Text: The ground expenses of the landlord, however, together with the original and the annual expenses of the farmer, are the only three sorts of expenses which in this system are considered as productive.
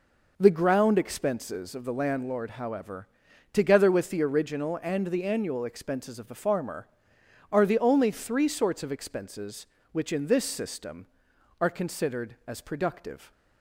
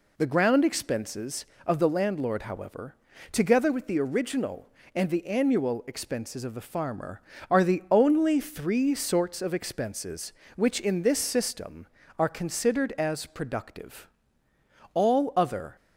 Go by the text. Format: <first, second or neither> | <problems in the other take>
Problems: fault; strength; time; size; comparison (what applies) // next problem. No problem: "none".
first | goes on to say "All other"; noticeable; from 14.9 s on; 0.82 s long